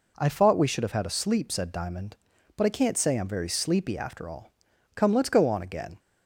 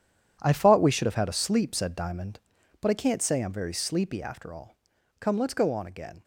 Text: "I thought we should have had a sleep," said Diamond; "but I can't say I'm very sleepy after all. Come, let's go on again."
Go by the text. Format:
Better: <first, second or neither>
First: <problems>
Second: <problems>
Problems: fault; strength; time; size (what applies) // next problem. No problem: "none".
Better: first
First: none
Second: gets quieter; strong; throughout; 12.5 dB